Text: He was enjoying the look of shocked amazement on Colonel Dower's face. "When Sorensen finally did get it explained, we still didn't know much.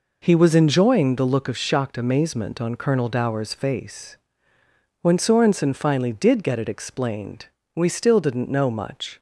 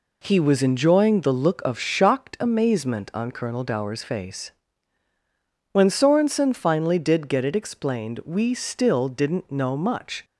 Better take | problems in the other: neither | none

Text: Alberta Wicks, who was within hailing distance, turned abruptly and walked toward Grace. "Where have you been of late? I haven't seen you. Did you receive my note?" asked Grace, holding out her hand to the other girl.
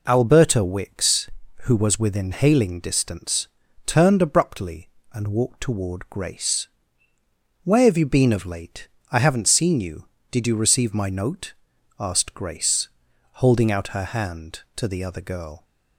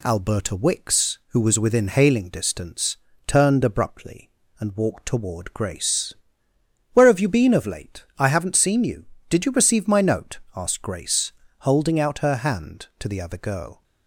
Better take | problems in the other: neither | none

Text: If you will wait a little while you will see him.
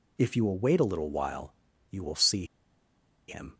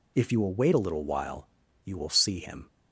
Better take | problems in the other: second | pauses between "while" and "you"; at 1.5 s; 0.38 s long; also in the second // pauses between "see" and "him"; noticeable; at 2.4 s; 0.83 s long

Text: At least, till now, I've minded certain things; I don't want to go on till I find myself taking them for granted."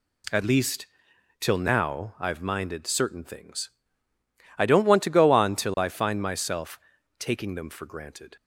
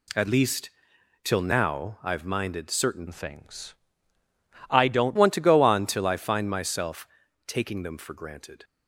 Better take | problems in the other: first | changes voice from "things" to "don't"; from 3.0 to 5.1 s; 2.1 s long // pauses between "myself" and "taking"; at 7.0 s; 0.40 s long; also in the first

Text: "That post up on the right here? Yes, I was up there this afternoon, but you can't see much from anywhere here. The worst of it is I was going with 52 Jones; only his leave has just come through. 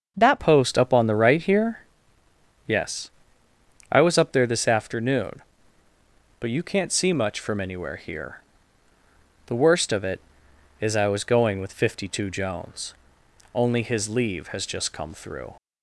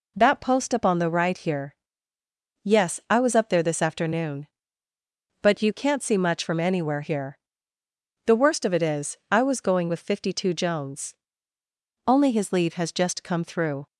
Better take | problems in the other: second | starts louder than the rest; until 1.1 s; 7 dB // changes voice at "post"; from 0.3 s on; 15.2 s long

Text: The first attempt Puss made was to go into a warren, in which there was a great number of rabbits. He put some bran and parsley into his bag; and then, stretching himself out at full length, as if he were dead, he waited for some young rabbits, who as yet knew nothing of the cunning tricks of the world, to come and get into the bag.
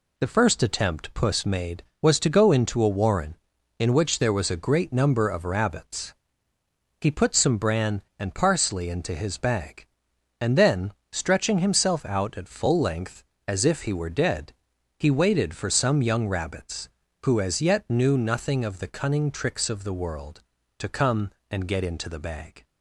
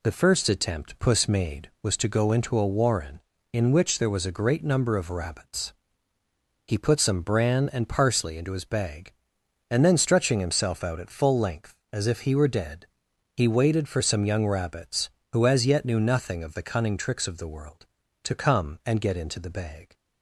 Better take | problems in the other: neither | none

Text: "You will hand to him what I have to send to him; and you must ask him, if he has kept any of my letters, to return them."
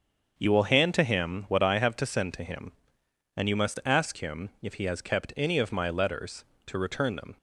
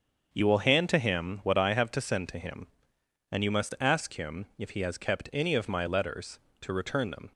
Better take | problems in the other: neither | starts louder than the rest; the same in both

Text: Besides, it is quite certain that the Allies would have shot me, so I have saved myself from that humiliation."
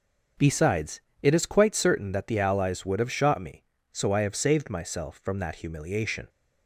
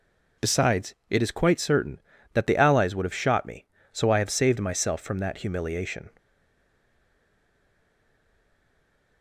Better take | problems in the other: first | stays silent after the last word; strong; from 6.1 s on; 3.1 s long

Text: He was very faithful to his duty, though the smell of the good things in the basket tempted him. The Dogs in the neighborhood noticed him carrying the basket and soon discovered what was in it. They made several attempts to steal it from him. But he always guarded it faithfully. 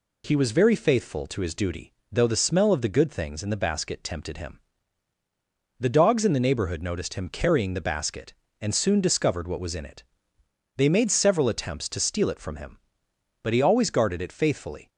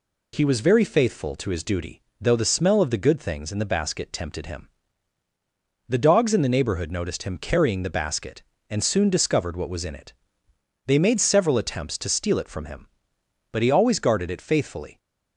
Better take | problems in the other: neither | none

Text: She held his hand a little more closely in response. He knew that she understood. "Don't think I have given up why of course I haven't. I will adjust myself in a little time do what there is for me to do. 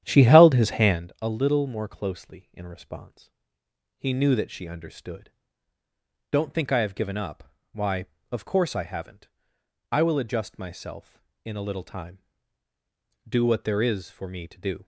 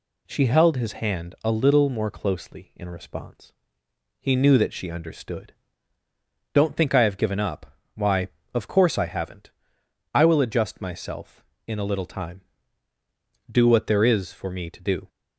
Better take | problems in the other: second | starts louder than the rest; strong; until 1.0 s; 10.5 dB // pauses between "up" and "why"; slight; at 7.5 s; 0.18 s long; slight in the second

